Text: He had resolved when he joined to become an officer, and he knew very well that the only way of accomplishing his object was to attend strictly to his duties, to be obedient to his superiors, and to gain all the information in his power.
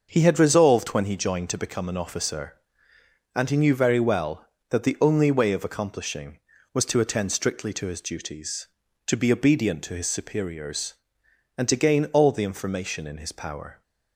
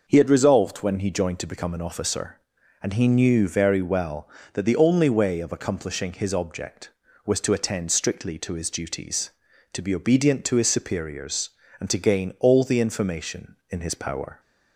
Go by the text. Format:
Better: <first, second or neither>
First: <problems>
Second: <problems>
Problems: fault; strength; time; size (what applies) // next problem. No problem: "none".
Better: second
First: starts louder than the rest; until 1.1 s; 6.5 dB // skips "his object"; at 6.5 s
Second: none